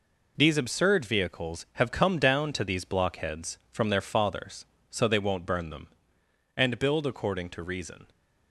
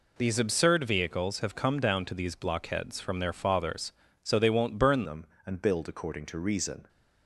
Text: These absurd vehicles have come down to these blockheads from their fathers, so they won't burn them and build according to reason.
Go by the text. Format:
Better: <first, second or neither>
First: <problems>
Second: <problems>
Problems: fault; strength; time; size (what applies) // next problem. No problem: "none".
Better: first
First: none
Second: changes voice at "them"; from 5.0 s on; 1.8 s long